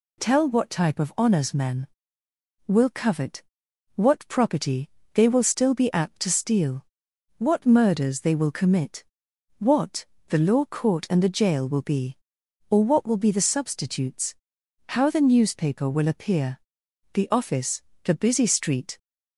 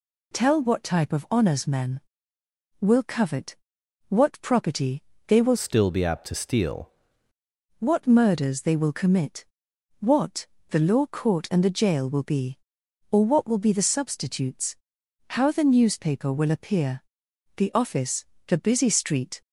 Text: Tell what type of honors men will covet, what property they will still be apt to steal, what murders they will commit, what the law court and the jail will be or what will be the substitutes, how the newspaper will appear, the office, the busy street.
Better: first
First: pauses between "property" and "they"; slight; at 4.8 s; 0.24 s long // pauses between "what" and "the"; slight; at 10.0 s; 0.24 s long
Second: pauses between "property" and "they"; slight; at 5.0 s; 0.24 s long // changes voice from "still" to "steal"; from 5.5 to 6.8 s; 1.3 s long // pauses between "what" and "the"; slight; at 10.4 s; 0.24 s long

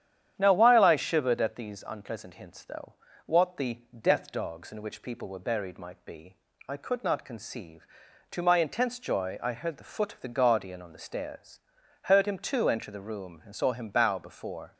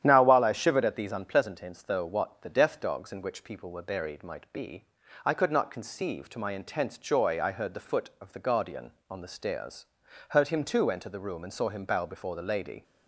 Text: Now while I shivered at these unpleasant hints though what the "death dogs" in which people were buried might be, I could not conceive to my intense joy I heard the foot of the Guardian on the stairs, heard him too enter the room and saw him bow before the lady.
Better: second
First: starts louder than the rest; strong; until 1.3 s; 9.5 dB // pauses between "though" and "what"; slight; at 2.9 s; 0.32 s long // pauses between "the" and "death"; slight; at 3.8 s; 0.16 s long // stops before "the lady"; at 14.7 s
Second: starts louder than the rest; strong; until 1.0 s; 10.5 dB

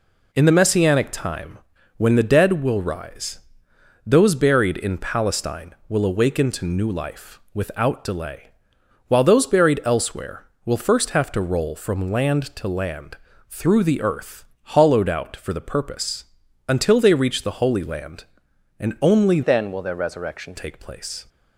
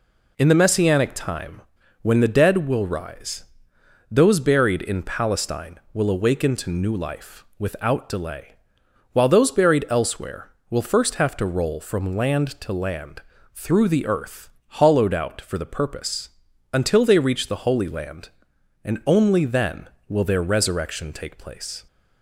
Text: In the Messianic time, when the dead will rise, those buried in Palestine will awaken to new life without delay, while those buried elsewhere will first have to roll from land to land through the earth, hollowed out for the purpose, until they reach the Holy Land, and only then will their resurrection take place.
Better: second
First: pauses between "land" and "through"; slight; at 13.1 s; 0.32 s long // changes voice from "then" to "resurrection"; from 19.4 to 20.5 s; 1.1 s long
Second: pauses between "land" and "through"; slight; at 13.2 s; 0.32 s long

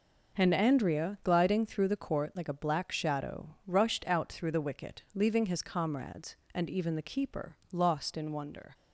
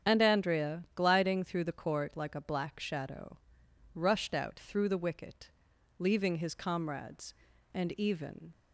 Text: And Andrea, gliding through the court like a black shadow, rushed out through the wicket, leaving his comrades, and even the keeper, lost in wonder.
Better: first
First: none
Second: starts louder than the rest; strong; until 1.1 s; 9 dB // stops before "the keeper lost in wonder"; at 8.5 s

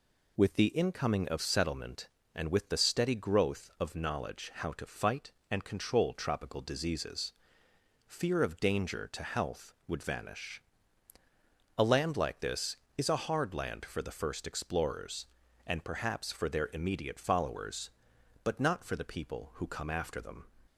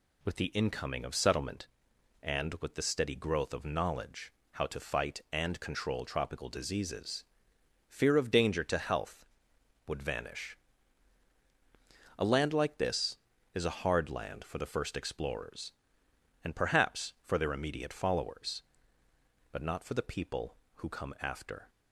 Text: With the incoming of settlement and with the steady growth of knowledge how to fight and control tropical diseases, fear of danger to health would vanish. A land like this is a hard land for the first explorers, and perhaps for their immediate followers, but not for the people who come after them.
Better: first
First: none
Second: pauses between "knowledge" and "how"; slight; at 4.3 s; 0.22 s long // stops before "them"; at 21.6 s

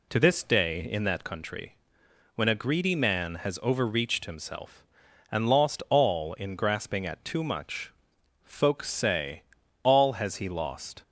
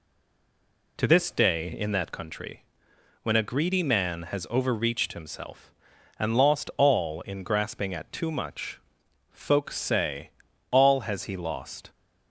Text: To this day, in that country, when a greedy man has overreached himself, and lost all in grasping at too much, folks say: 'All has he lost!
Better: first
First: none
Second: stays silent before the first word; slight; until 0.9 s; 0.9 s long

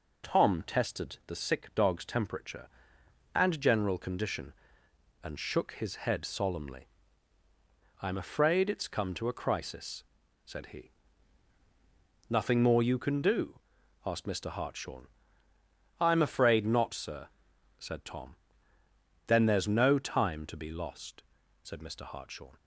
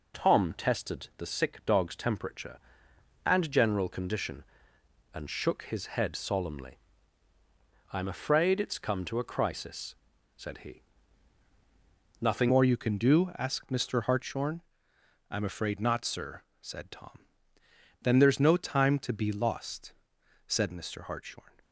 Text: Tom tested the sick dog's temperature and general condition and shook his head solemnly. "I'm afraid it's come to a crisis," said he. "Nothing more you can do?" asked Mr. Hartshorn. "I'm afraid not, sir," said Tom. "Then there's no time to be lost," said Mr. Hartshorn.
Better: first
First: none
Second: changes voice at "more"; from 12.4 s on; 9.1 s long

